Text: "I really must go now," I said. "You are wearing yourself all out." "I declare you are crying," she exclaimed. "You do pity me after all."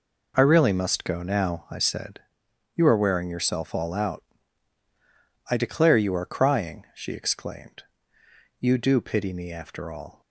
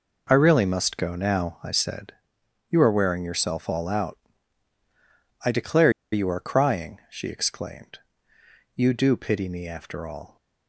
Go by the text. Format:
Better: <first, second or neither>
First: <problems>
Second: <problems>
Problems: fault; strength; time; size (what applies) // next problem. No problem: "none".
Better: first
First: none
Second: pauses between "declare" and "you"; slight; at 5.8 s; 0.22 s long